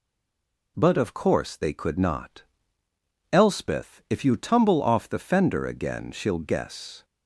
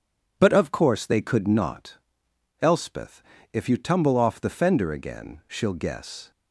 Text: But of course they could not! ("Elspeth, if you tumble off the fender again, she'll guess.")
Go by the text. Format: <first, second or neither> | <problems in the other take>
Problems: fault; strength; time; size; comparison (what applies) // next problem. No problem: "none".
second | stays silent before the first word; slight; until 0.7 s; 0.7 s long